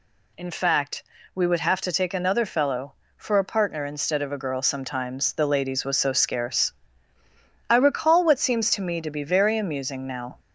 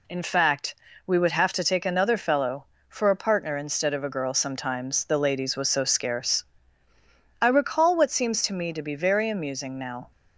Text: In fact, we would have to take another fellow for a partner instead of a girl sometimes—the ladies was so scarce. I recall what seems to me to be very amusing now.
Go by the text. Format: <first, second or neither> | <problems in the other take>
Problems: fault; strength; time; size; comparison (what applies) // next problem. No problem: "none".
second | gets louder; slight; throughout; 2 dB